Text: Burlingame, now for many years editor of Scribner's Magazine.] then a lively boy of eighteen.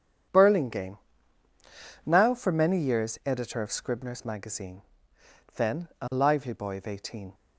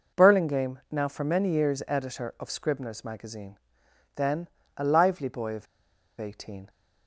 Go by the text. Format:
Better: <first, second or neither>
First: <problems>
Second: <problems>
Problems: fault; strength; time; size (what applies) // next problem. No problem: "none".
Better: first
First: none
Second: pauses between "then" and "a"; slight; at 4.4 s; 0.28 s long // pauses between "of" and "eighteen"; noticeable; at 5.6 s; 0.55 s long